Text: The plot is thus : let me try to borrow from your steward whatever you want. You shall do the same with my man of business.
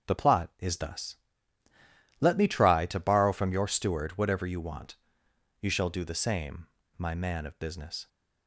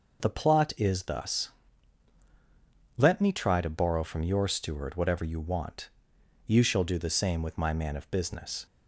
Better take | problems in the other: second | starts louder than the rest; until 1.1 s; 7 dB // skips "with"; at 6.8 s

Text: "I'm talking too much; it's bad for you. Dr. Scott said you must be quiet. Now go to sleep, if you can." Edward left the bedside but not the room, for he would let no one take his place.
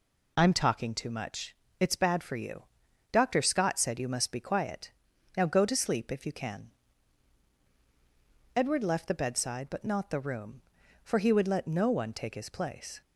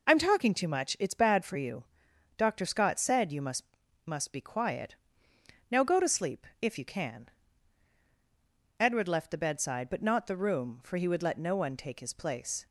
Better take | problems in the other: first | says "must" twice; at 4.0 s

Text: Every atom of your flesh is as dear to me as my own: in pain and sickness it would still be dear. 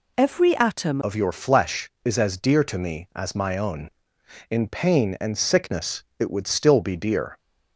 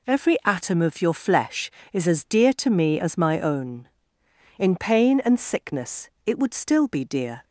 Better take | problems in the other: second | changes voice at "of"; from 1.0 s on; 6.3 s long // pauses between "sickness" and "it"; slight; at 6.0 s; 0.16 s long; slight in the second

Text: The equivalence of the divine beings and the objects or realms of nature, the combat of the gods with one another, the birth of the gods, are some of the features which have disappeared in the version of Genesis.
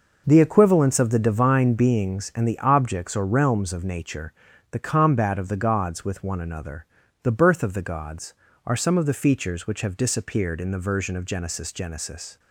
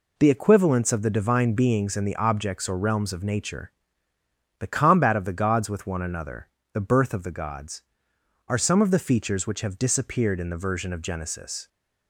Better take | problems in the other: second | says "Genesis" twice; at 11.7 s

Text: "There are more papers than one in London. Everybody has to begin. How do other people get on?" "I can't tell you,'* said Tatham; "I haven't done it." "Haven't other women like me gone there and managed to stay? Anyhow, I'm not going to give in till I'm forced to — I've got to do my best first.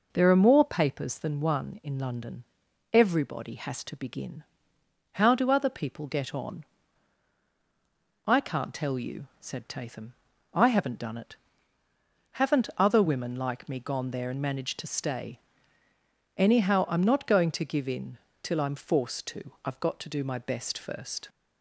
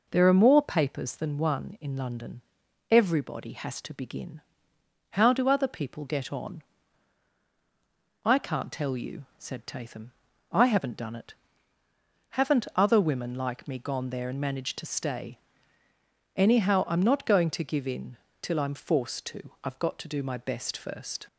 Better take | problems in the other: neither | pauses between "in" and "till"; slight; the same in both

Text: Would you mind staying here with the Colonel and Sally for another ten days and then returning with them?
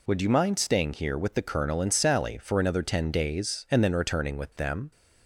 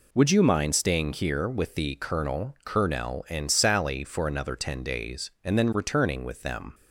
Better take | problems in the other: first | says "Colonel" twice; at 2.6 s

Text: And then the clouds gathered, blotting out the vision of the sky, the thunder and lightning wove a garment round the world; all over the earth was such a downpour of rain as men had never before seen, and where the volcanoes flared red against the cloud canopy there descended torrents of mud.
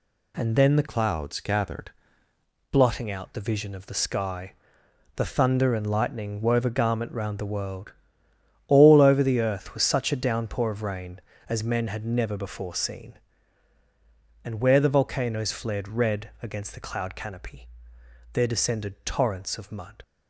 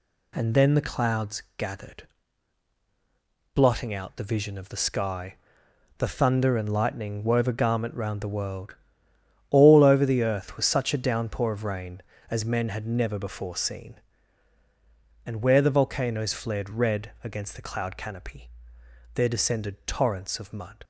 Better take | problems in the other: second | changes voice from "clouds" to "gathered"; from 0.8 to 1.9 s; 1.1 s long // pauses between "canopy" and "there"; noticeable; at 17.6 s; 0.64 s long; noticeable in the second

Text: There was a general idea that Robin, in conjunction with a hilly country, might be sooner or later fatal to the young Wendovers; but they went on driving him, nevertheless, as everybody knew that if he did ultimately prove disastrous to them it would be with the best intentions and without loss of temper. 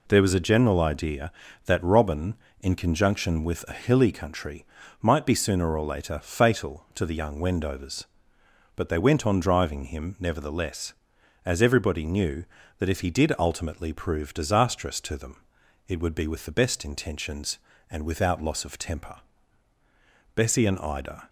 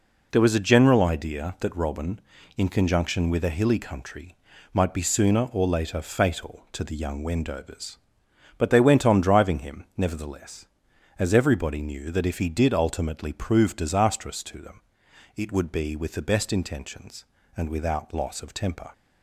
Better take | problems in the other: second | pauses between "them" and "it"; noticeable; at 15.4 s; 0.46 s long; noticeable in the second // goes on to say "Bessie and Ida"; noticeable; from 20.3 s on; 0.92 s long

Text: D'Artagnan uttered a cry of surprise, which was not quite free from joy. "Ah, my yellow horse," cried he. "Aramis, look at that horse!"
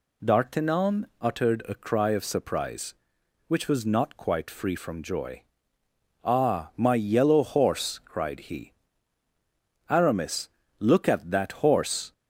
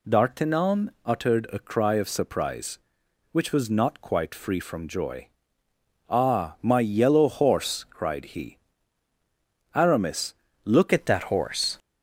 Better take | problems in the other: first | changes voice at "at"; from 10.9 s on; 0.8 s long

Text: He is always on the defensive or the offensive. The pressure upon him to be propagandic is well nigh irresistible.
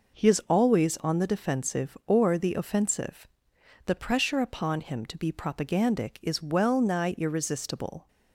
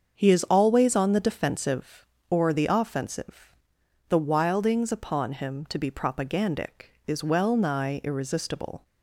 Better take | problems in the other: first | starts louder than the rest; until 1.1 s; 7 dB // says "wildings" for "pressure"; at 4.1 s

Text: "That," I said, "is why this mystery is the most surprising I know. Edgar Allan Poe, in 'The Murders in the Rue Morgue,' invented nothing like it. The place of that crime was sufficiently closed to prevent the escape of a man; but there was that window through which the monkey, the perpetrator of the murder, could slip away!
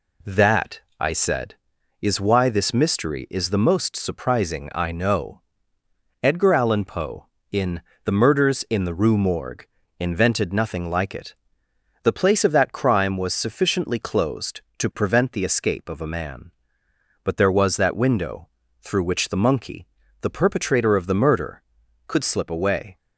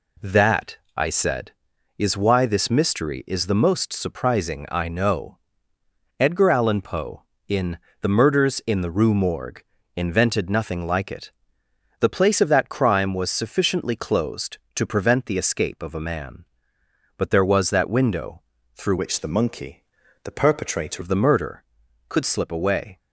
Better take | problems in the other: first | pauses between "in" and "The"; slight; at 7.7 s; 0.22 s long; slight in the first // pauses between "window" and "through"; slight; at 18.4 s; 0.32 s long; slight in the first // changes voice from "which" to "perpetrator"; from 18.9 to 21.0 s; 2.1 s long

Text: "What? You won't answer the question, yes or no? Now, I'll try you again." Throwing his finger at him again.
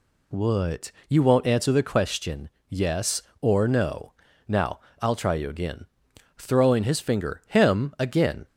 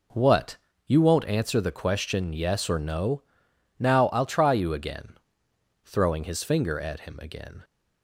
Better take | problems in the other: second | skips "at"; at 7.4 s

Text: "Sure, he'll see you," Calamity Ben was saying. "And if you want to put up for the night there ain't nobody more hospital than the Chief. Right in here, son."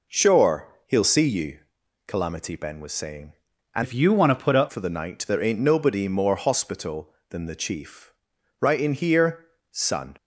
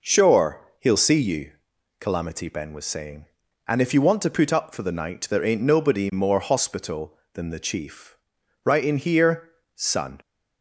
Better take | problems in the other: second | changes voice from "if" to "up"; from 3.8 to 4.7 s; 0.9 s long

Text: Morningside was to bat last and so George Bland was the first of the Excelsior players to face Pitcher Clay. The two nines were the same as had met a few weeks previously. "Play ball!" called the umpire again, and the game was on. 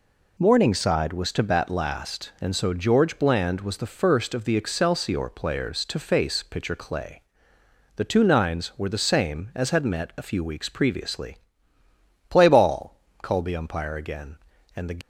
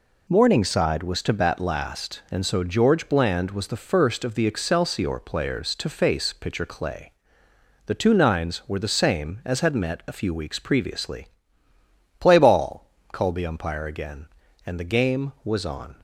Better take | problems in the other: second | stops before "game was on"; at 15.0 s

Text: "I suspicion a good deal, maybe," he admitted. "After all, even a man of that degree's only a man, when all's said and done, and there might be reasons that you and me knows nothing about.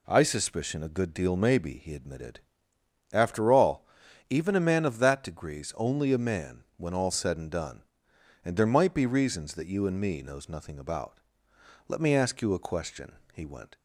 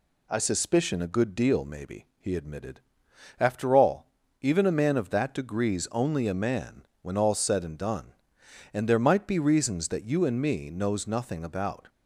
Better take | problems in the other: second | goes on to say "Let me ask you a question he went"; strong; from 11.8 s on; 1.9 s long

